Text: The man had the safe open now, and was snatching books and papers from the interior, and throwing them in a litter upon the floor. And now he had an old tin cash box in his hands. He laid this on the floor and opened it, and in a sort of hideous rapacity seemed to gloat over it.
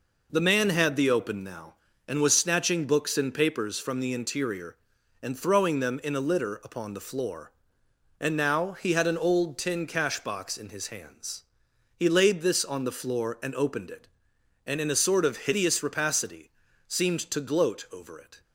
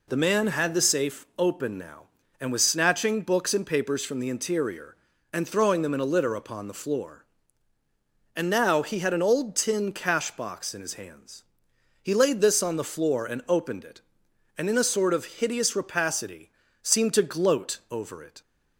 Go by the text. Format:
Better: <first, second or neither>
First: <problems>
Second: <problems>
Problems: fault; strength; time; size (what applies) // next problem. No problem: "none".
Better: second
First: skips "safe"; at 1.1 s // pauses between "rapacity" and "seemed"; slight; at 16.5 s; 0.36 s long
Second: pauses between "rapacity" and "seemed"; slight; at 16.4 s; 0.32 s long